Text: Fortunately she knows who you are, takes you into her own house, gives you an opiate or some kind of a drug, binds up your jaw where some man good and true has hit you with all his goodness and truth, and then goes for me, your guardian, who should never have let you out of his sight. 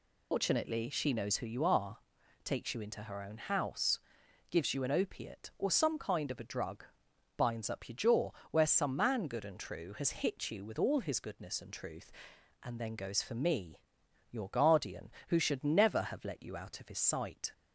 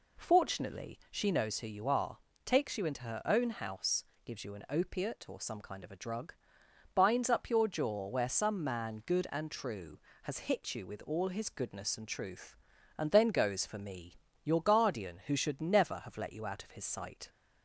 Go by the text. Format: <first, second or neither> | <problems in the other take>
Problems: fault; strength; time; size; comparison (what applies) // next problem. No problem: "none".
second | loses the start of "Fortunately"; at 0.3 s; 150 ms // pauses between "jaw" and "where"; slight; at 8.3 s; 0.20 s long